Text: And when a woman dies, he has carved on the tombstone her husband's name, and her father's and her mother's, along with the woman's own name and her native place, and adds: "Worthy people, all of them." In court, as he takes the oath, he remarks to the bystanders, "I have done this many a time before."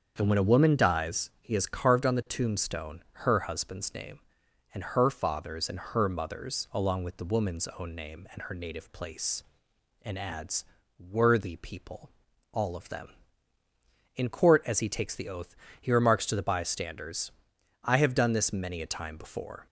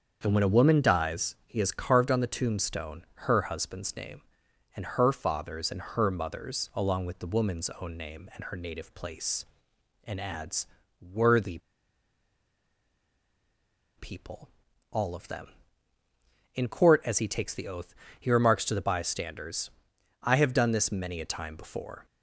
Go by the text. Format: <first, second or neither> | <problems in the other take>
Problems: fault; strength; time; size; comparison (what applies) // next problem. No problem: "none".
first | starts louder than the rest; until 1.2 s; 7 dB; also in the first // pauses between "Worthy" and "people"; strong; at 11.5 s; 2.3 s long